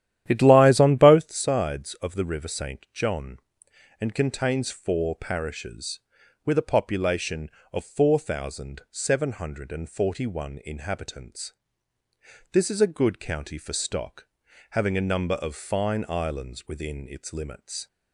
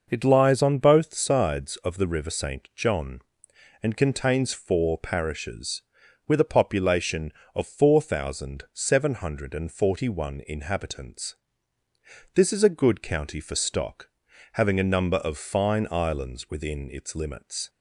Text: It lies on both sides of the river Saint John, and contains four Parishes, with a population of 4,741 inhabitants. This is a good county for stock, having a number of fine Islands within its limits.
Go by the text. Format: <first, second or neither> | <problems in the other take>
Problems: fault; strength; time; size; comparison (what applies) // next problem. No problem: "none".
second | starts louder than the rest; strong; until 1.2 s; 11.5 dB